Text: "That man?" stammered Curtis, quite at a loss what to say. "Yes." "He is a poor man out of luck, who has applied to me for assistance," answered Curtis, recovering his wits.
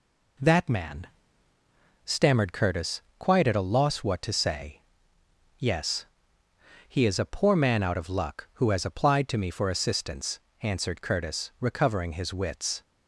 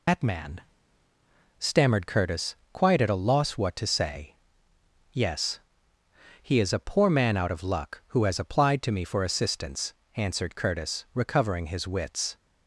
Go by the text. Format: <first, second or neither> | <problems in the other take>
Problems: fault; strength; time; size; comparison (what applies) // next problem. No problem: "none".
first | loses the start of "That"; at 0.0 s; 140 ms